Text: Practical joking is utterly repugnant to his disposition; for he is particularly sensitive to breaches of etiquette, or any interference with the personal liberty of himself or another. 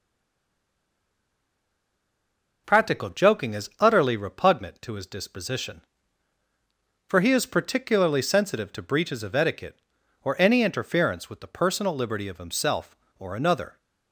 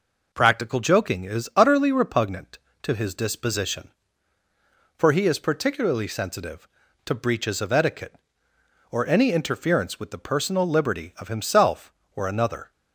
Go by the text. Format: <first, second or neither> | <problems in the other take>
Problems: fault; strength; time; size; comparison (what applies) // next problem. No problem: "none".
second | stays silent before the first word; strong; until 2.6 s; 2.6 s long